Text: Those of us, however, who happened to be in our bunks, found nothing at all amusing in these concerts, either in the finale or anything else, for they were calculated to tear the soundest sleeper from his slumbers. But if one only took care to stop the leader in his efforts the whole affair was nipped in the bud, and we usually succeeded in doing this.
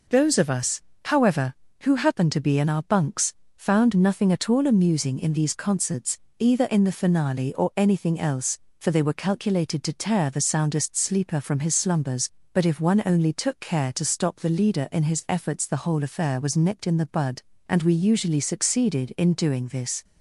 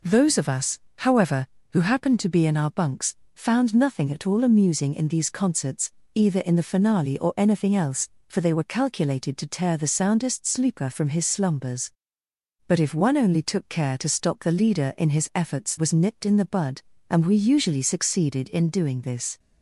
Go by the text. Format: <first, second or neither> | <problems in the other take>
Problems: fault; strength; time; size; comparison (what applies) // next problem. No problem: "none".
first | skips "the whole affair"; at 15.7 s